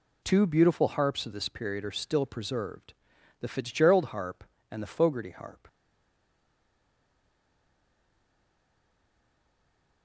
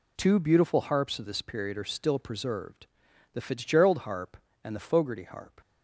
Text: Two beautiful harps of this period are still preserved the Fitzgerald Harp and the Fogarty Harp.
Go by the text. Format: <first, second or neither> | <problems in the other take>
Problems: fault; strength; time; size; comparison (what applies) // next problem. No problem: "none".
second | pauses between "preserved" and "the"; noticeable; at 2.9 s; 0.48 s long; noticeable in the second // stays silent after the last word; strong; from 5.6 s on; 4.4 s long